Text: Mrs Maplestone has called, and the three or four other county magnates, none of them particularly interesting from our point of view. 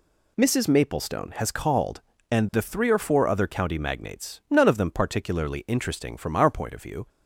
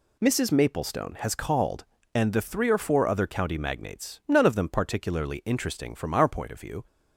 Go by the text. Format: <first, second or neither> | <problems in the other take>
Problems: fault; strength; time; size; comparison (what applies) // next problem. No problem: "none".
neither | none